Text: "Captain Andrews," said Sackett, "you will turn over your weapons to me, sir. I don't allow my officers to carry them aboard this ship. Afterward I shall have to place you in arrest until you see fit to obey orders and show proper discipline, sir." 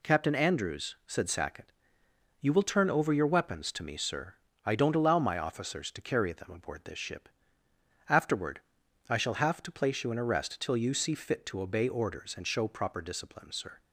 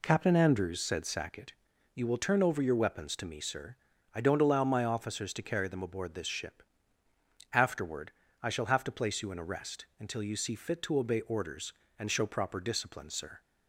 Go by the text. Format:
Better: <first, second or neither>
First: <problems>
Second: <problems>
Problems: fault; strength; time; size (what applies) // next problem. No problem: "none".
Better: second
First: pauses between "Afterward" and "I"; noticeable; at 8.6 s; 0.48 s long // says "till" for "until"; at 10.5 s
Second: pauses between "Afterward" and "I"; slight; at 8.1 s; 0.30 s long